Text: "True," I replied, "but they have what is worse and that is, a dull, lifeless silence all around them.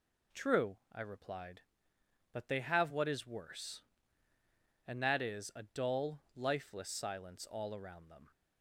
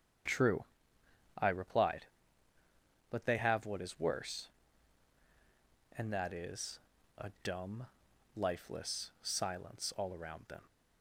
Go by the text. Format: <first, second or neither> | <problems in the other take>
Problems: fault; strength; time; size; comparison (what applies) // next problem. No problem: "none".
first | starts louder than the rest; strong; until 1.9 s; 8 dB // says "dumb" for "dull"; at 7.4 s